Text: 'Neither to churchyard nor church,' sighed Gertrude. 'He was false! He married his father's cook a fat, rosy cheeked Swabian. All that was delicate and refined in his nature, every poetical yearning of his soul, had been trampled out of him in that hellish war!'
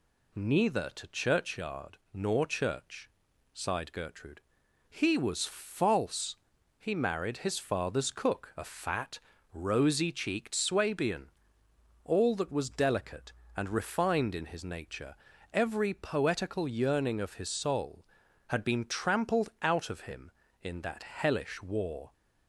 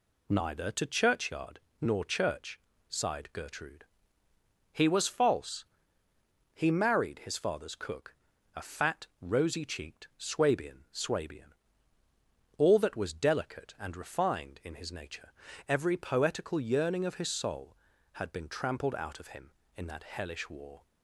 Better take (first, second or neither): first